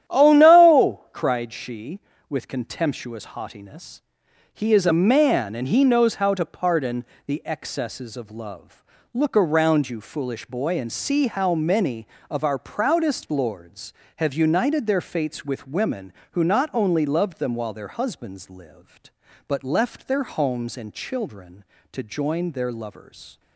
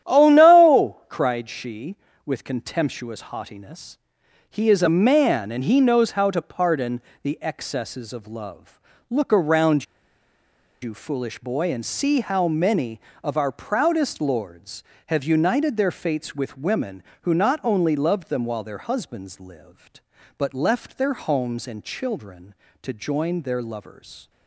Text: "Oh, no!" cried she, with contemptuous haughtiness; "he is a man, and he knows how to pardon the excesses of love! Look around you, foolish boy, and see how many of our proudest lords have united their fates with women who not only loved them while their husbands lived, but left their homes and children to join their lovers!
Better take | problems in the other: first | starts louder than the rest; strong; until 1.1 s; 11 dB; strong in the first // pauses between "pardon" and "the"; slight; at 7.0 s; 0.22 s long; slight in the first // pauses between "around" and "you"; noticeable; at 9.8 s; 0.97 s long

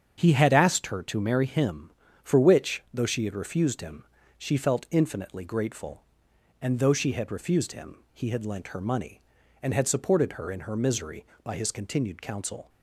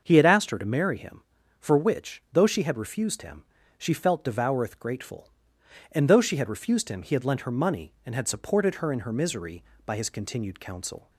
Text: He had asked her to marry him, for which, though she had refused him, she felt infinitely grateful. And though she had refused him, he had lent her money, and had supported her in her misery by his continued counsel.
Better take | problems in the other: first | starts louder than the rest; until 1.0 s; 6.5 dB; strong in the first // says "devoureth" for "infinitely"; at 4.2 s

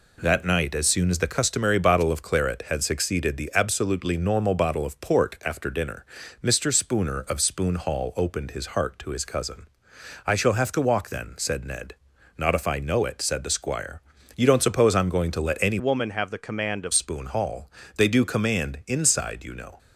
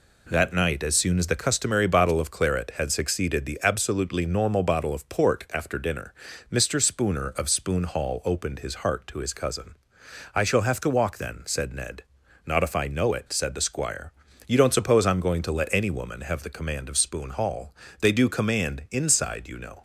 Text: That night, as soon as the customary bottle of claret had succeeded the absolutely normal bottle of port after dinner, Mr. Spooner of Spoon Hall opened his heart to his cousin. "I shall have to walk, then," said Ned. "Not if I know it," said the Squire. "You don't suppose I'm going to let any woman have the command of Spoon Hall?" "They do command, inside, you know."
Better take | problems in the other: second | changes voice from "woman" to "of"; from 15.7 to 16.9 s; 1.2 s long

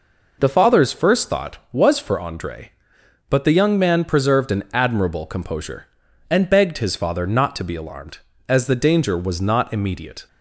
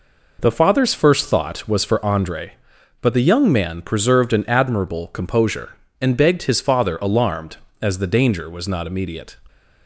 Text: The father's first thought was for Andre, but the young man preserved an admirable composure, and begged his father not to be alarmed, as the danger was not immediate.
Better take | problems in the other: first | skips "not to be"; at 6.9 s

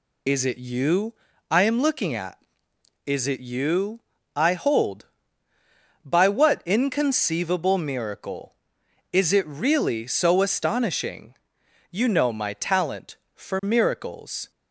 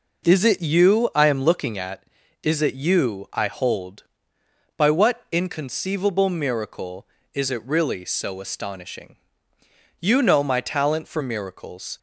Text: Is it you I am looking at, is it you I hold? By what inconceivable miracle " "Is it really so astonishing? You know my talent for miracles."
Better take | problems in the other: second | loses the start of "Is"; at 0.2 s; 25 ms // pauses between "you" and "I"; at 1.1 s; 0.38 s long // pauses between "you" and "I"; slight; at 3.9 s; 0.36 s long

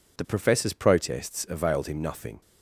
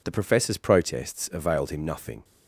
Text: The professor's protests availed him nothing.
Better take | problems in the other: neither | none

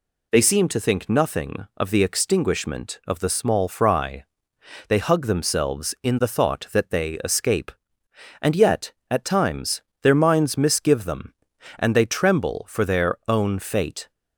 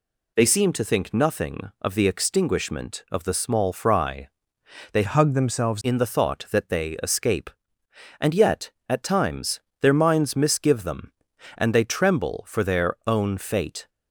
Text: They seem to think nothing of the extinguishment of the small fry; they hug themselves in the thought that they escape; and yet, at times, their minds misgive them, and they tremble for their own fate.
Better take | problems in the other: first | changes voice from "hug" to "themselves"; from 5.0 to 5.8 s; 0.8 s long

